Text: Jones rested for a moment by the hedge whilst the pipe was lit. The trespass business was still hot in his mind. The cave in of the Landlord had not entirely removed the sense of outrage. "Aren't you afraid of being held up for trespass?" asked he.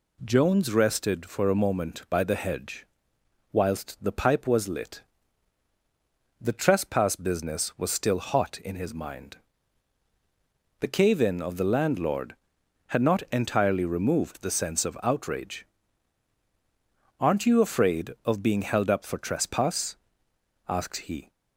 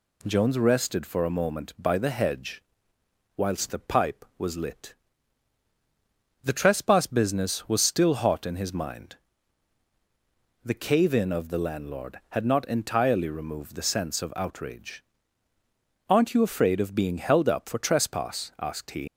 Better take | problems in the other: first | pauses between "hedge" and "whilst"; noticeable; at 2.6 s; 0.74 s long; noticeable in the first // leaves "he" unfinished; at 19.0 s; 85 ms

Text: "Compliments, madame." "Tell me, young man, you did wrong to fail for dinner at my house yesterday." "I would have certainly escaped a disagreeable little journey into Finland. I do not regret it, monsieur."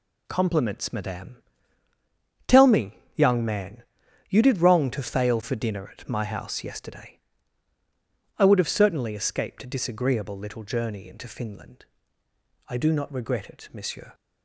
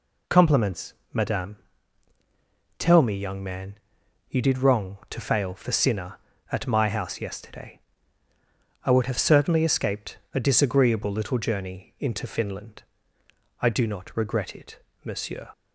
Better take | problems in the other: first | says "sinner" for "dinner"; at 5.7 s // pauses between "escaped" and "a"; slight; at 10.1 s; 0.16 s long

